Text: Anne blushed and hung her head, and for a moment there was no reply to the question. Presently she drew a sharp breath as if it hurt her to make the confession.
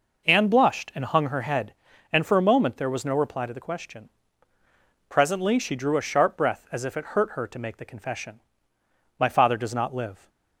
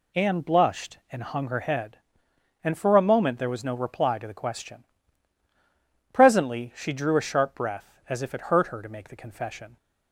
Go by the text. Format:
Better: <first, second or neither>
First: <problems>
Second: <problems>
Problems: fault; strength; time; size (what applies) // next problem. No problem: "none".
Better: second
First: goes on to say "My father does not live"; noticeable; from 9.1 s on; 1.1 s long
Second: none